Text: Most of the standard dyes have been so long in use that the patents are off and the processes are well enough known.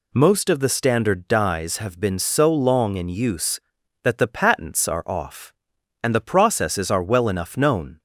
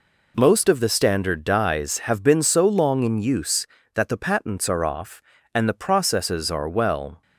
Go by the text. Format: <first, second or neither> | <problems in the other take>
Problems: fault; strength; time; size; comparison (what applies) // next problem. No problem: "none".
first | stops before "enough known"; at 7.2 s